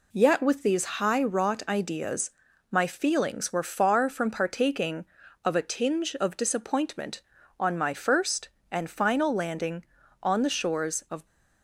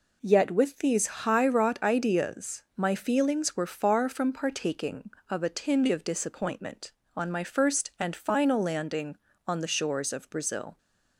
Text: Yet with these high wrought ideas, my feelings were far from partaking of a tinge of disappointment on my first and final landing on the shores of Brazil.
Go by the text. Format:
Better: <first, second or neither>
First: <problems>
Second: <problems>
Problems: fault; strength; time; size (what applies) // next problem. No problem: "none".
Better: second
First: stops before "Brazil"; at 11.2 s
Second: none